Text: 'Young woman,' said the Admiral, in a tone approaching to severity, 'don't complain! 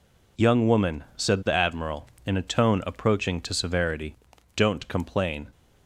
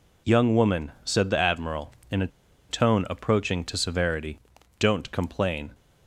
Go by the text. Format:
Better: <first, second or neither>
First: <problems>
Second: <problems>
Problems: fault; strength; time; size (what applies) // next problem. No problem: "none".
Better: first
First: none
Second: pauses between "a" and "tone"; at 2.2 s; 0.41 s long